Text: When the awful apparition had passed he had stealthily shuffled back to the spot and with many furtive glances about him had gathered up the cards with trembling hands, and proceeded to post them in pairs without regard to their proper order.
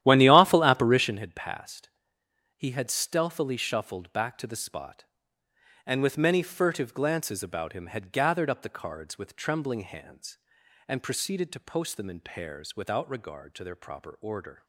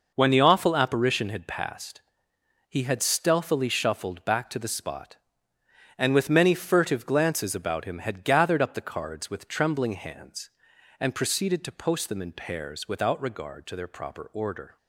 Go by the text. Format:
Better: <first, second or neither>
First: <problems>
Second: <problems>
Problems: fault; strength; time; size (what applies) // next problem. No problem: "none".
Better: second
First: starts louder than the rest; strong; until 1.2 s; 12 dB // pauses between "passed" and "he"; noticeable; at 1.8 s; 0.68 s long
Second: pauses between "passed" and "he"; noticeable; at 2.0 s; 0.68 s long